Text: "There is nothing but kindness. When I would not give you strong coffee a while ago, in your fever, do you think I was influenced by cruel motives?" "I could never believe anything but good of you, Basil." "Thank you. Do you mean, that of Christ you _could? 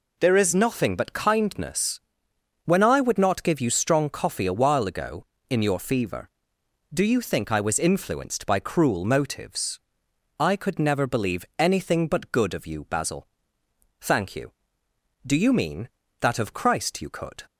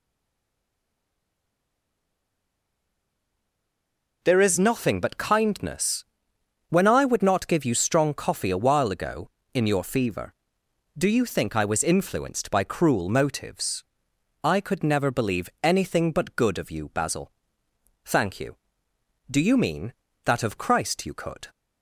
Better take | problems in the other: first | stays silent before the first word; strong; until 4.2 s; 4.2 s long

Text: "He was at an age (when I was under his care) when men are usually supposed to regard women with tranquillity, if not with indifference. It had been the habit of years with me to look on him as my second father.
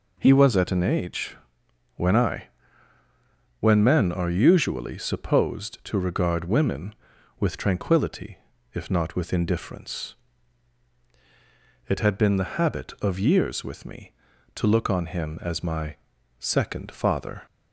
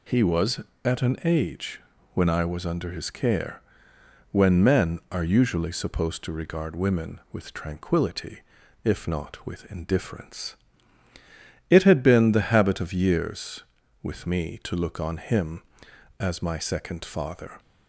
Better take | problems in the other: second | skips "was under his care"; at 3.0 s // pauses between "my" and "second"; at 15.9 s; 0.44 s long

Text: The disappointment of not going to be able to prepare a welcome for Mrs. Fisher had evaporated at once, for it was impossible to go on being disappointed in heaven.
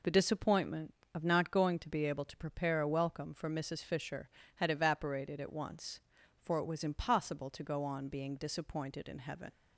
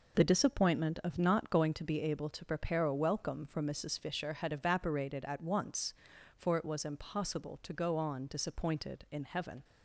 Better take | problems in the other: first | skips "being"; at 8.2 s

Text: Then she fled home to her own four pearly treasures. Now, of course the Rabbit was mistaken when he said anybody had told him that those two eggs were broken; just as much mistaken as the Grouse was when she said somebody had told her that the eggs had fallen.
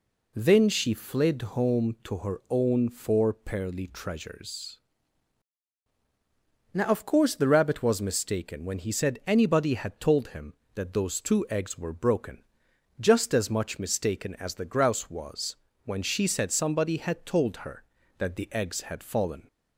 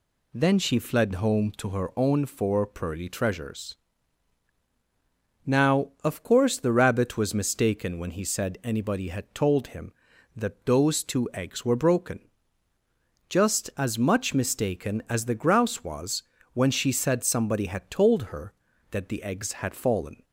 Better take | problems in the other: neither | pauses between "was" and "when"; slight; the same in both

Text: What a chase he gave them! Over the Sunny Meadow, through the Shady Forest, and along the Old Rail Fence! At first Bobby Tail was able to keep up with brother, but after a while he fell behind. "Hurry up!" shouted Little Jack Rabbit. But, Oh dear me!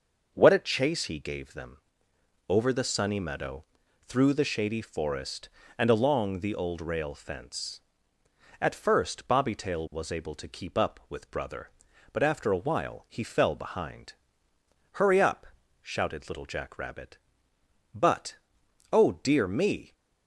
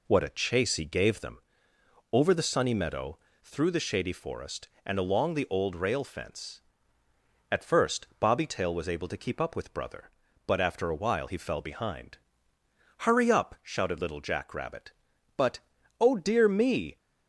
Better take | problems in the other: neither | none

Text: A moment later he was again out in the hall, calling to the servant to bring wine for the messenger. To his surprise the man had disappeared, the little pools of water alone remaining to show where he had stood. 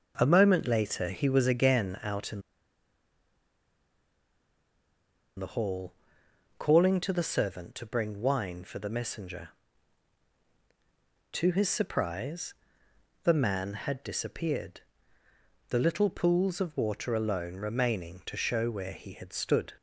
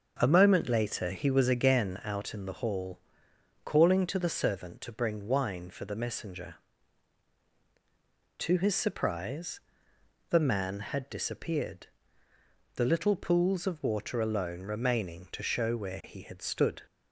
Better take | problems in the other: second | starts louder than the rest; until 1.1 s; 6.5 dB; also in the second // pauses between "in" and "the"; strong; at 2.4 s; 2.9 s long // pauses between "surprise" and "the"; noticeable; at 12.5 s; 0.70 s long; noticeable in the second

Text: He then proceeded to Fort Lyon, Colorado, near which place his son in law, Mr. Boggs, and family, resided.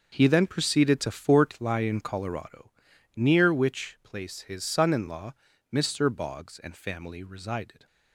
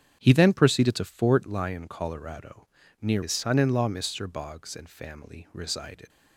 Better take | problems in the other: first | starts louder than the rest; strong; until 1.2 s; 8.5 dB // skips "which place"; at 3.2 s

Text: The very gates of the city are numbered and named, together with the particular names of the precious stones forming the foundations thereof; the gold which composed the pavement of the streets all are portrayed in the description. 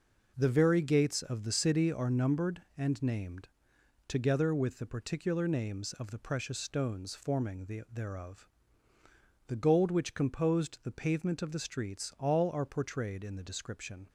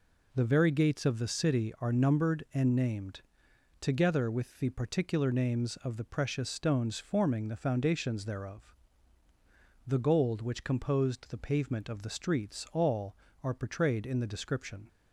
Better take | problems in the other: second | skips "foundations"; at 7.8 s

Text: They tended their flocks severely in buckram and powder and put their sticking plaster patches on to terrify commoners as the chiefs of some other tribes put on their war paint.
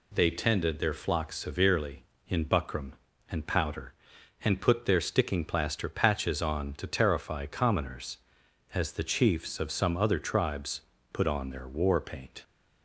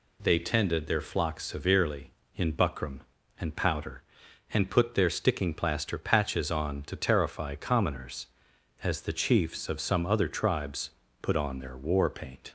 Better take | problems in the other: neither | pauses between "tribes" and "put"; slight; the same in both

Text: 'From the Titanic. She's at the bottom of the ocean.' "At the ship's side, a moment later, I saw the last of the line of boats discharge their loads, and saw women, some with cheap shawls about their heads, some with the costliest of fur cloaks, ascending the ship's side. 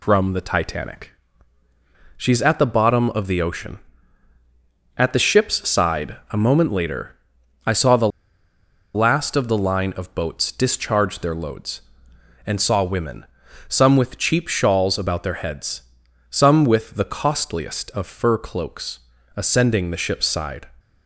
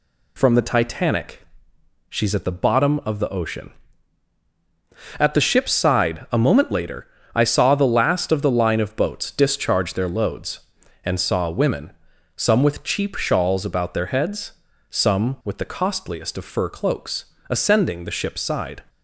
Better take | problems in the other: second | pauses between "the" and "last"; noticeable; at 8.0 s; 0.85 s long

